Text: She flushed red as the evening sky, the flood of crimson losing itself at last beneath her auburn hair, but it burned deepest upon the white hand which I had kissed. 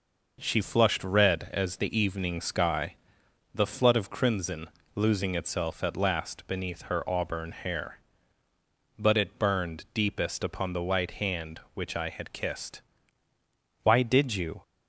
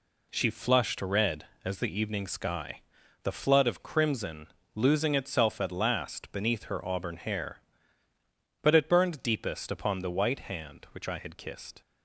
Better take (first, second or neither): second